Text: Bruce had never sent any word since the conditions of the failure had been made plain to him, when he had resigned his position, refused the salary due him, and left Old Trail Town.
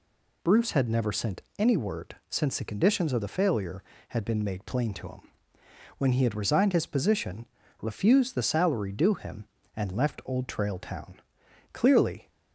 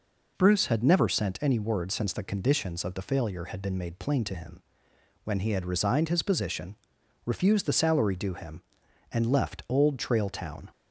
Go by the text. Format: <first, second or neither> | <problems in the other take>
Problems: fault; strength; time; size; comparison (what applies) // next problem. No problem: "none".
second | pauses between "sent" and "any"; slight; at 1.4 s; 0.16 s long // goes on to say "Clearly"; from 11.7 s on; 0.56 s long